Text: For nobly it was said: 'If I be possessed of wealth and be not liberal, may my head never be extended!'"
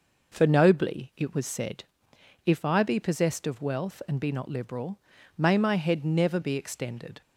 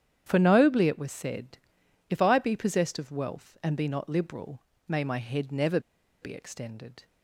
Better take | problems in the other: first | starts louder than the rest; strong; until 1.2 s; 9.5 dB // pauses between "never" and "be"; at 5.7 s; 0.42 s long

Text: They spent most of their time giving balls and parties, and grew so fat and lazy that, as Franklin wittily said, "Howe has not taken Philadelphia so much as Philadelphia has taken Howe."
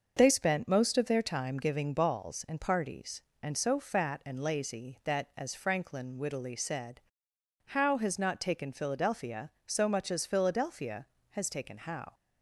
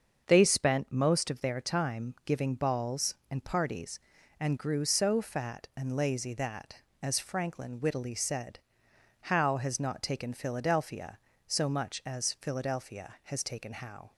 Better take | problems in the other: second | starts louder than the rest; until 1.1 s; 6.5 dB; also in the second // skips "grew"; at 3.5 s

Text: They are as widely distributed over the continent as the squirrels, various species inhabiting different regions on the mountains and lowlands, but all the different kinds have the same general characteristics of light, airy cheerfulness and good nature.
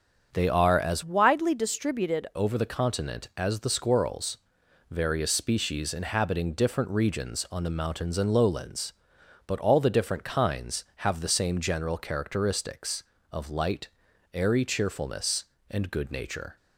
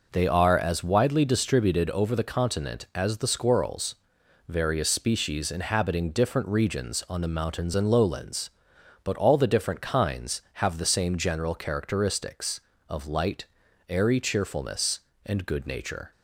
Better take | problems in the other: second | starts louder than the rest; strong; until 1.3 s; 7.5 dB // changes voice from "widely" to "distributed"; from 1.0 to 2.2 s; 1.2 s long

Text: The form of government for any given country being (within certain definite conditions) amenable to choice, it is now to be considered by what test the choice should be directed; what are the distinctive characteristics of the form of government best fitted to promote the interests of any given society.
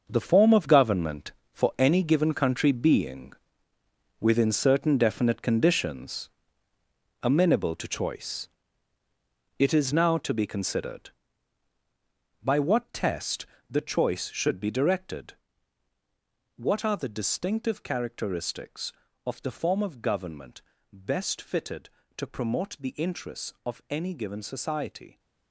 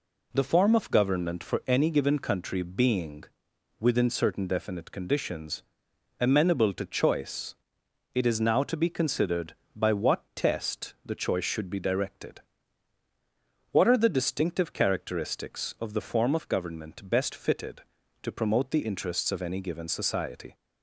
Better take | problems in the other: second | gets quieter; strong; throughout; 11 dB // pauses between "test" and "the"; slight; at 13.4 s; 0.24 s long // pauses between "government" and "best"; slight; at 20.6 s; 0.32 s long

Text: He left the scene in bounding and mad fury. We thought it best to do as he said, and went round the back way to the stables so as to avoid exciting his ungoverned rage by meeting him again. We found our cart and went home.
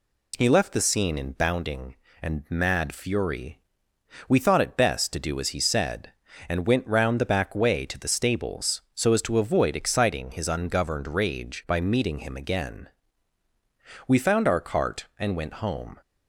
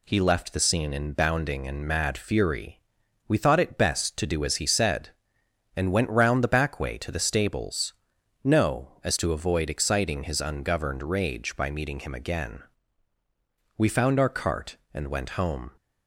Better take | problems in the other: first | says "no" for "so"; at 8.4 s

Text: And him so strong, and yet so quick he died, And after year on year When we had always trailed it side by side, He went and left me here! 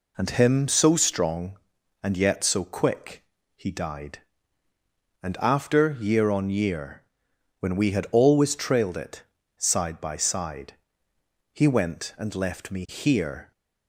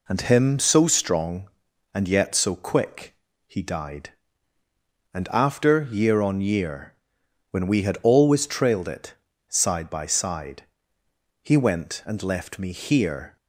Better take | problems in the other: neither | pauses between "quick" and "he"; slight; the same in both // pauses between "year" and "When"; noticeable; the same in both // pauses between "it" and "side"; slight; the same in both

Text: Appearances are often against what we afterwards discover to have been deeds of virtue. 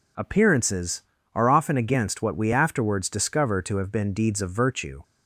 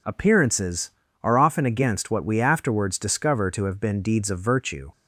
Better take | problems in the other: neither | none

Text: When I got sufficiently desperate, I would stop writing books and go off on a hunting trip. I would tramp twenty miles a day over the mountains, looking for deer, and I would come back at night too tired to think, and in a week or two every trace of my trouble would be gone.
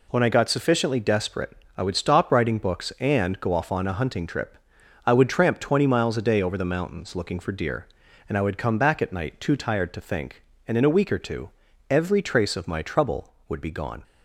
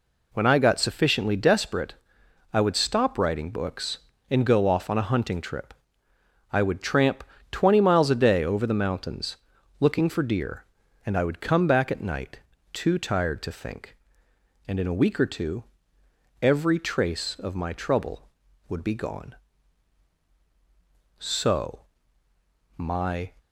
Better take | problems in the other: first | pauses between "tramp" and "twenty"; slight; at 7.2 s; 0.26 s long // pauses between "night" and "too"; slight; at 12.3 s; 0.32 s long // pauses between "two" and "every"; noticeable; at 15.6 s; 0.78 s long; also in the first // goes on to say "So my"; strong; from 21.1 s on; 2.1 s long

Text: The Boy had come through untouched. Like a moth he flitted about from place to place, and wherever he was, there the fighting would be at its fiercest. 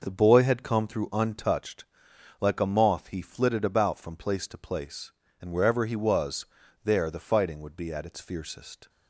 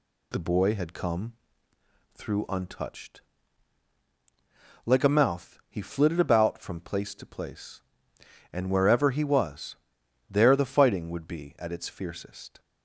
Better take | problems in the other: first | pauses between "come" and "through"; noticeable; at 1.3 s; 0.82 s long // says "mouth" for "moth"; at 5.0 s

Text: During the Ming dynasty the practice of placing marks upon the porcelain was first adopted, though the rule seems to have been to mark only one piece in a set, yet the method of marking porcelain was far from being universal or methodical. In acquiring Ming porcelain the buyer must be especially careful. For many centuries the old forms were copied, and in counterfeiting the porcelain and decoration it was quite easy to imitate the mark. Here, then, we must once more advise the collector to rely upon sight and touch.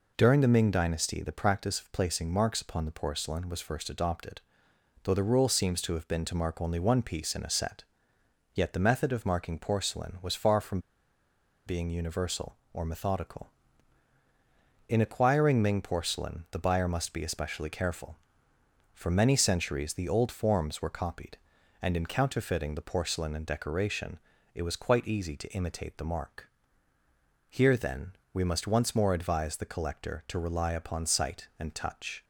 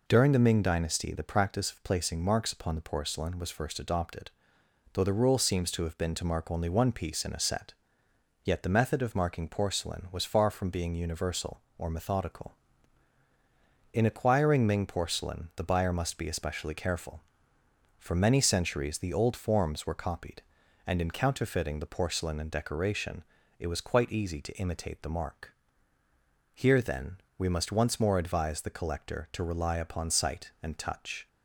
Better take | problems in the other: second | pauses between "from" and "being"; noticeable; at 10.7 s; 0.87 s long // pauses between "decoration" and "it"; slight; at 24.1 s; 0.34 s long; slight in the second

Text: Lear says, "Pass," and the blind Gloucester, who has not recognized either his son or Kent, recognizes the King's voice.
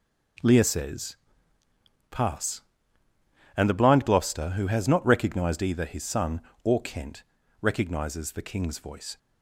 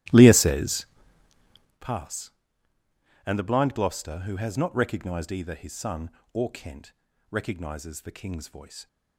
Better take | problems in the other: first | starts louder than the rest; strong; until 1.9 s; 15.5 dB

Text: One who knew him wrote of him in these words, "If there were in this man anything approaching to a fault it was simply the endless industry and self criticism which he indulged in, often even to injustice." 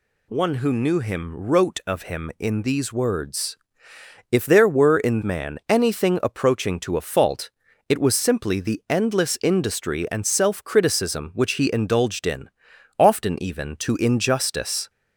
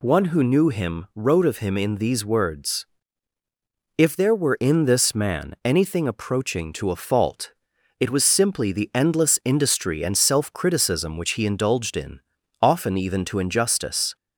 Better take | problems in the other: second | skips "this"; at 5.2 s // pauses between "fault" and "it"; at 7.4 s; 0.40 s long; noticeable in the second

